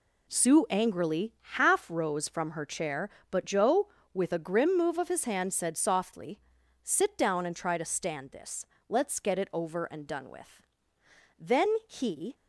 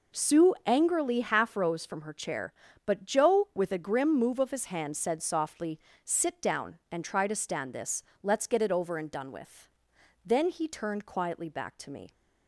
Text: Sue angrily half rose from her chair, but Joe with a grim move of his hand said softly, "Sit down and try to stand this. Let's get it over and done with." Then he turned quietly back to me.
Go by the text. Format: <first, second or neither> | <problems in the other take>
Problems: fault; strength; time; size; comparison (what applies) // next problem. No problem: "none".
second | pauses between "angrily" and "half"; slight; at 1.3 s; 0.22 s long // stops before "turned quietly back to me"; at 12.3 s